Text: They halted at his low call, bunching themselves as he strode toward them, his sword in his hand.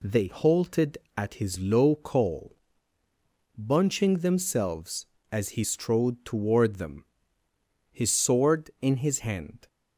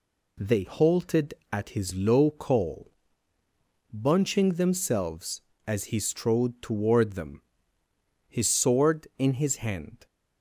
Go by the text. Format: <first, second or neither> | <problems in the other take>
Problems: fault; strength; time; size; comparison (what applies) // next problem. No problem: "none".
neither | none